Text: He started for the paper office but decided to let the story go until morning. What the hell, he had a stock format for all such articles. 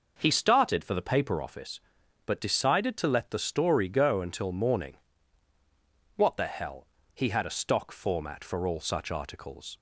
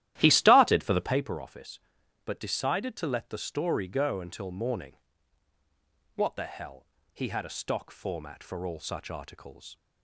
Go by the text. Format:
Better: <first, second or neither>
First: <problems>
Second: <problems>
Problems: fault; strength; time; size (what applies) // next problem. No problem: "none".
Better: first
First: none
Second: starts louder than the rest; strong; until 1.2 s; 13.5 dB